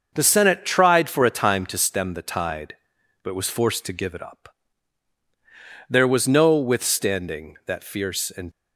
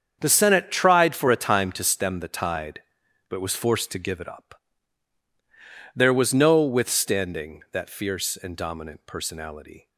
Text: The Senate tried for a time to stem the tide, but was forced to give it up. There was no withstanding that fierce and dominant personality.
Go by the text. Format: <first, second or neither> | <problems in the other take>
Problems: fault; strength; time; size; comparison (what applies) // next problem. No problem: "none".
second | starts louder than the rest; until 1.1 s; 6.5 dB; strong in the second // stops before "dominant personality"; at 8.5 s